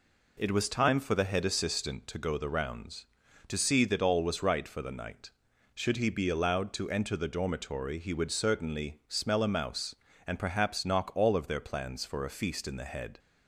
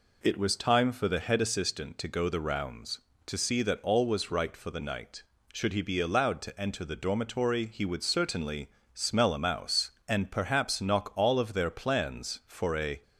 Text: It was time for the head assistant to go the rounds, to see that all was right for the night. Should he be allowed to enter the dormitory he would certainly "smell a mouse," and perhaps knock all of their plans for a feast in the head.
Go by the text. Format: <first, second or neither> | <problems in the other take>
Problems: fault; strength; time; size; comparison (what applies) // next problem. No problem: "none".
first | pauses between "certainly" and "smell"; slight; at 8.6 s; 0.26 s long // stops before "feast in the head"; at 13.0 s